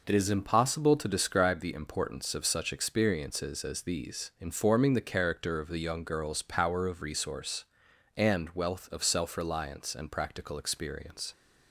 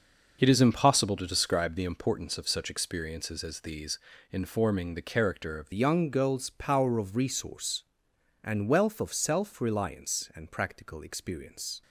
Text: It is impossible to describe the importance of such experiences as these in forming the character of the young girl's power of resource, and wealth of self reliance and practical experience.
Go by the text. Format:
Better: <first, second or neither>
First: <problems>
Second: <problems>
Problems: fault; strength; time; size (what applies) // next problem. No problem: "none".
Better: first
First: none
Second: changes voice at "young"; from 5.7 s on; 6.1 s long